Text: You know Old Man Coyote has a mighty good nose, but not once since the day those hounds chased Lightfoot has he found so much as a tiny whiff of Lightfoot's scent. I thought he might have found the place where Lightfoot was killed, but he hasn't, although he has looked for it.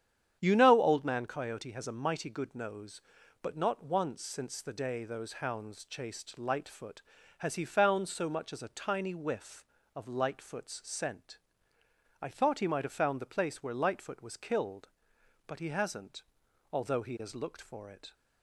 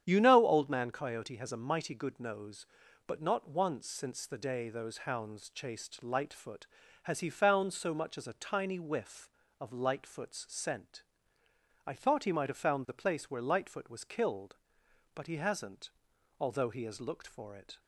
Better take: neither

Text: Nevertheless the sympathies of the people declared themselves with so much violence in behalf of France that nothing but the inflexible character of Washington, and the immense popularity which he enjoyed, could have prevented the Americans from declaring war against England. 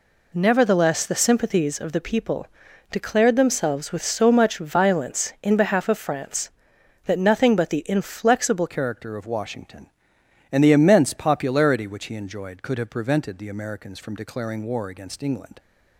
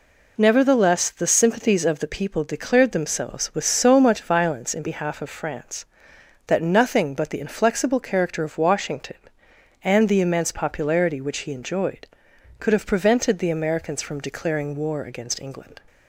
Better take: second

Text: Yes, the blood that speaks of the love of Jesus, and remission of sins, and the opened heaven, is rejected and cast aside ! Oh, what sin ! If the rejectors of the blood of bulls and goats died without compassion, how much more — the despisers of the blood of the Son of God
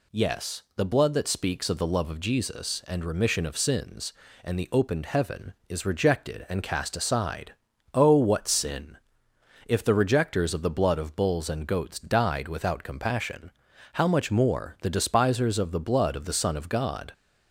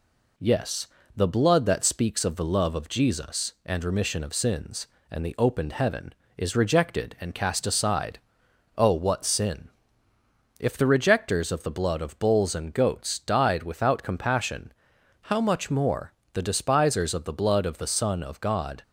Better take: neither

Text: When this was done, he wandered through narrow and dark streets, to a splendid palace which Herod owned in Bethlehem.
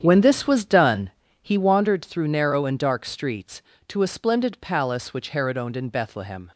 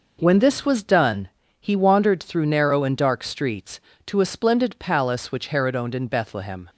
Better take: second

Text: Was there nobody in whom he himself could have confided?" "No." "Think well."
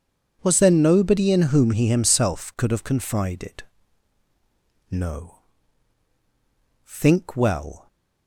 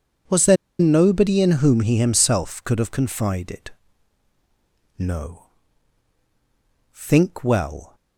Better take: first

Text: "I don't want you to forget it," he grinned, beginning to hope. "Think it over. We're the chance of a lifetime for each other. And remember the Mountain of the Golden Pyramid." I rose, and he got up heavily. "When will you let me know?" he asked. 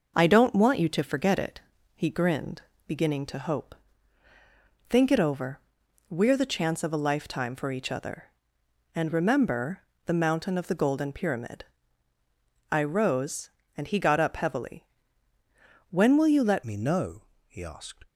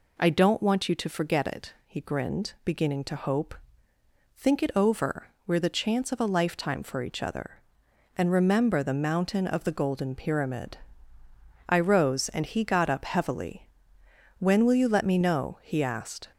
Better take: second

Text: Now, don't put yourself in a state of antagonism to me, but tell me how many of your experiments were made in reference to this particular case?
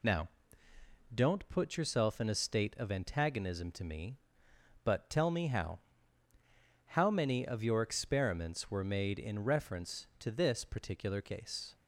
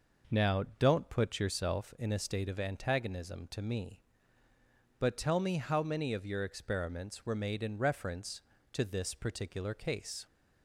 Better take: second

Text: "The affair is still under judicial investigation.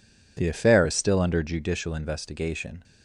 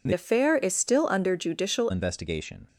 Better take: first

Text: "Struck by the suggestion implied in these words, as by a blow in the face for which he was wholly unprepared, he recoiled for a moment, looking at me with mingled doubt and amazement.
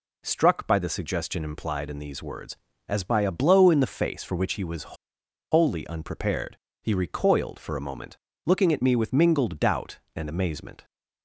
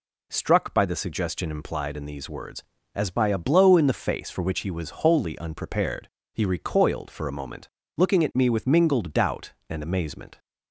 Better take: second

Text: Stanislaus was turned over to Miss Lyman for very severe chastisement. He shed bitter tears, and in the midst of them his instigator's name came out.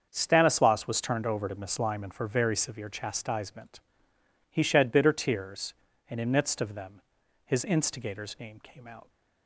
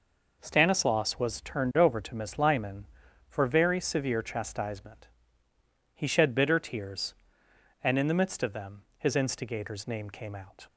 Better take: second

